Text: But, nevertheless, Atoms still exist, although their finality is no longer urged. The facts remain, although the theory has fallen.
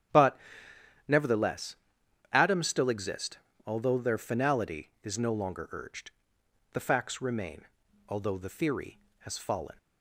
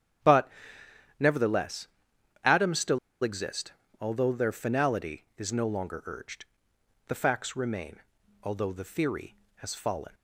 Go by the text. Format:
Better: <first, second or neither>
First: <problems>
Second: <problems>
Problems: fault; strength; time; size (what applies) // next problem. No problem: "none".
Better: first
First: starts louder than the rest; strong; until 2.4 s; 10.5 dB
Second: starts louder than the rest; strong; until 2.5 s; 10.5 dB // pauses between "still" and "exist"; slight; at 2.9 s; 0.25 s long